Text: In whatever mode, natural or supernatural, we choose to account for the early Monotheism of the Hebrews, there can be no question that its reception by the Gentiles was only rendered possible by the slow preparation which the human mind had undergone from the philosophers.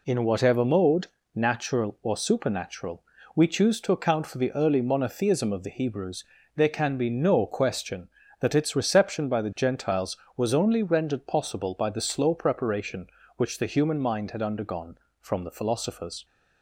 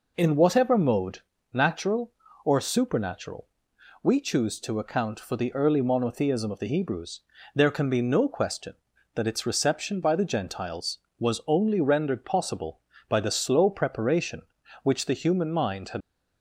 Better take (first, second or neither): first